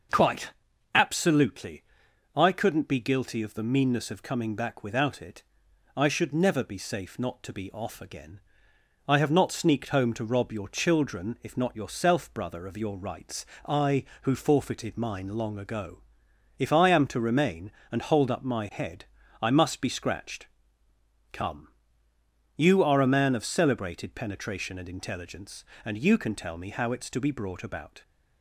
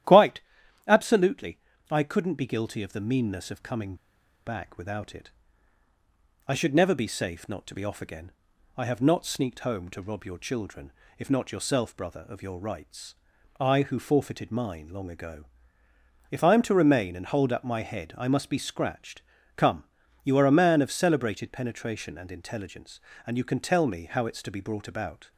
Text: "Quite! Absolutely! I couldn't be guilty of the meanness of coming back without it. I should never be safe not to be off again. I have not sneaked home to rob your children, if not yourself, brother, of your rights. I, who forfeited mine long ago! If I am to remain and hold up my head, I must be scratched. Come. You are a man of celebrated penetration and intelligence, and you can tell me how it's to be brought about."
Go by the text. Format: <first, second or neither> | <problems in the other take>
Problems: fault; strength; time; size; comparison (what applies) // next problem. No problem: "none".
first | starts louder than the rest; strong; until 1.5 s; 12 dB; also in the first // pauses between "coming" and "back"; noticeable; at 3.9 s; 0.51 s long